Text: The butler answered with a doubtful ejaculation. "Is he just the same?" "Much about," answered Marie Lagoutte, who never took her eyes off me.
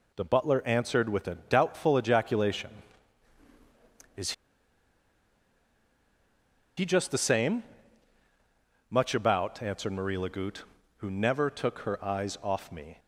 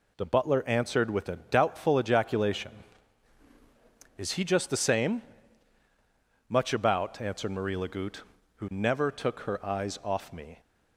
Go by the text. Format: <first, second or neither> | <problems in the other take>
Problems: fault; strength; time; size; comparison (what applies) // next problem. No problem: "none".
second | pauses between "Is" and "he"; strong; at 4.3 s; 2.4 s long